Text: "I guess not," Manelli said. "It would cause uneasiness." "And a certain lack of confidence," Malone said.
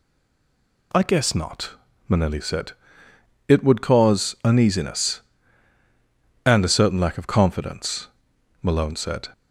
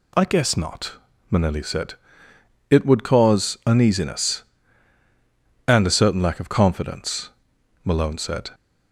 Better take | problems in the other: second | stays silent before the first word; slight; until 0.9 s; 0.9 s long

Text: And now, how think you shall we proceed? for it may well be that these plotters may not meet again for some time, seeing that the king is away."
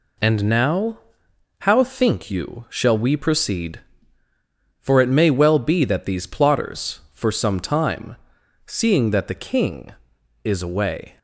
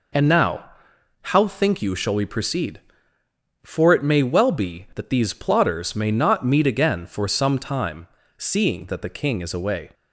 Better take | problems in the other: second | skips "may not meet again"; at 7.0 s

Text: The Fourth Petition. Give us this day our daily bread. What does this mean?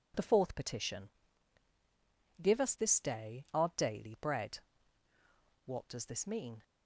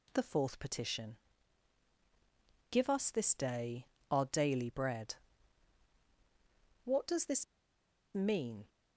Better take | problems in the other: first | pauses between "day" and "our"; slight; at 3.8 s; 0.24 s long // pauses between "this" and "mean"; noticeable; at 7.4 s; 0.69 s long

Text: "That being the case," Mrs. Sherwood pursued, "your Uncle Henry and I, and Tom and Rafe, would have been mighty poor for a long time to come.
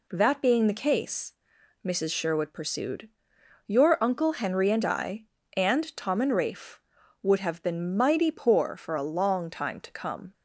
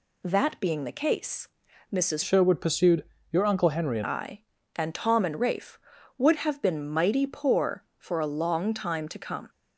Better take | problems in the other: first | changes voice from "Sherwood" to "and"; from 2.2 to 4.0 s; 1.8 s long

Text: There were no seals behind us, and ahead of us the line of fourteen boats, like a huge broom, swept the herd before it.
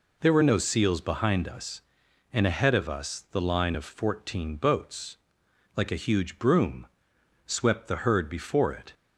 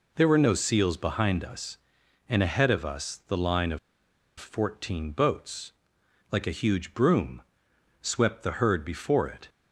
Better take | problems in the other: first | pauses between "of" and "fourteen"; noticeable; at 3.7 s; 0.60 s long

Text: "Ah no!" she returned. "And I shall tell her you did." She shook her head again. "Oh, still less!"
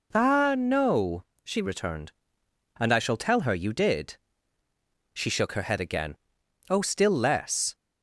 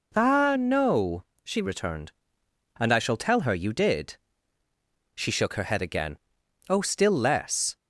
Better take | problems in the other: neither | none

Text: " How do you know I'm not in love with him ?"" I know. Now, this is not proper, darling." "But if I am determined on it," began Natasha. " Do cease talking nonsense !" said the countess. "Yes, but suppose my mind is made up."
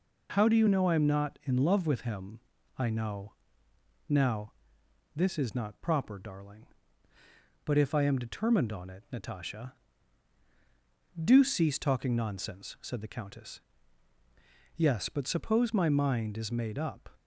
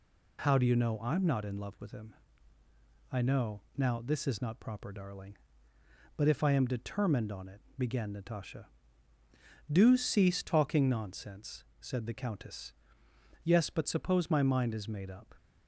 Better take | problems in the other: second | skips "began"; at 9.0 s

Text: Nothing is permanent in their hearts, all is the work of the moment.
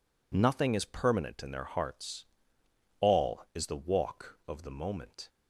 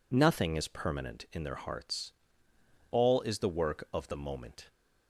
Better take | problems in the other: second | says "walk" for "work"; at 3.7 s

